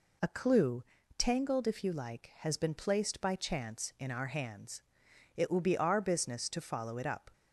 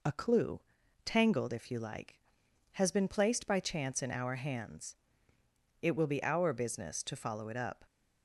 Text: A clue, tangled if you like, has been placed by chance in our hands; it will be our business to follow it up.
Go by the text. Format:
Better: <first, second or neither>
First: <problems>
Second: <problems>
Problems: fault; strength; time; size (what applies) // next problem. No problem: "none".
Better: neither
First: none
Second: none